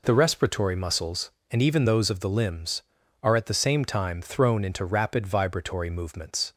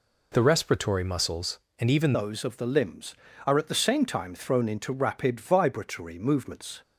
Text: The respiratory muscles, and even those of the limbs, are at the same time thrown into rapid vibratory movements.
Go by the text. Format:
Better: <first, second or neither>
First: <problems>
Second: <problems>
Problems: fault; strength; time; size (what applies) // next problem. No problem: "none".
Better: first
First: none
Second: changes voice at "those"; from 2.1 s on; 4.7 s long